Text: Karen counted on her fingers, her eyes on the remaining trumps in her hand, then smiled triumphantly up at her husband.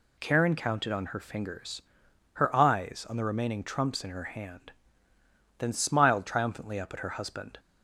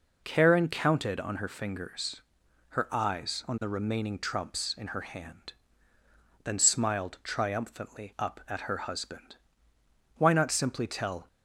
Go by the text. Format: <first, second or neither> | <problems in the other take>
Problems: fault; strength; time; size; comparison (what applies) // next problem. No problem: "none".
first | goes on to say "Why not simply tell"; noticeable; from 10.1 s on; 1.1 s long